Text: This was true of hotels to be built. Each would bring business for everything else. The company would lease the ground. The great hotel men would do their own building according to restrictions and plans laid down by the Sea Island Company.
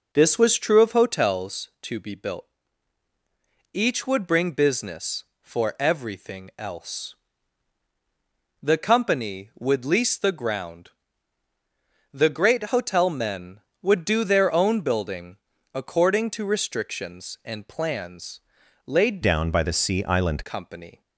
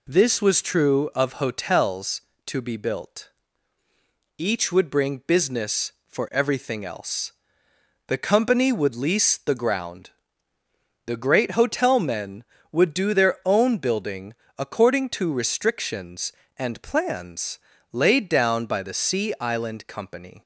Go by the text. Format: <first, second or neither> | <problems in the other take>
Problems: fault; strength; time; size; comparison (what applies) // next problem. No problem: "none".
second | pauses between "building" and "according"; at 15.3 s; 0.38 s long; slight in the second // pauses between "plans" and "laid"; noticeable; at 18.3 s; 0.46 s long; slight in the second // changes voice from "down" to "Island"; from 19.2 to 20.4 s; 1.2 s long